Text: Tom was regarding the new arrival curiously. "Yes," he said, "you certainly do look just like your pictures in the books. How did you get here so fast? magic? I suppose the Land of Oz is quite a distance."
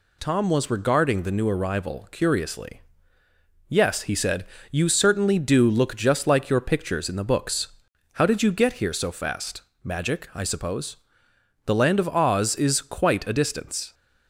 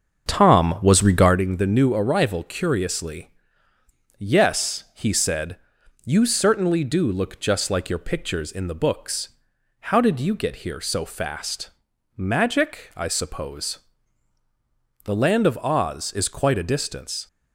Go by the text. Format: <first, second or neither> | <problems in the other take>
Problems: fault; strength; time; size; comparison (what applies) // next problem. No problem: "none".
first | starts louder than the rest; until 1.4 s; 7 dB // pauses between "suppose" and "the"; strong; at 13.7 s; 1.2 s long; noticeable in the first